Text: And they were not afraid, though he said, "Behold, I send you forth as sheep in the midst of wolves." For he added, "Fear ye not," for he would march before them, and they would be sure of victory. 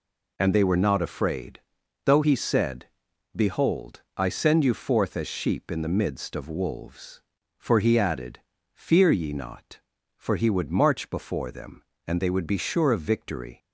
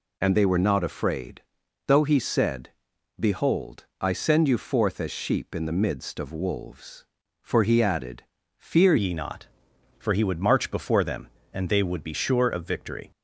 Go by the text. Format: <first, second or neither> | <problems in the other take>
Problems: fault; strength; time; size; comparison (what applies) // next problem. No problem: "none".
first | changes voice at "ye"; from 8.9 s on; 4.2 s long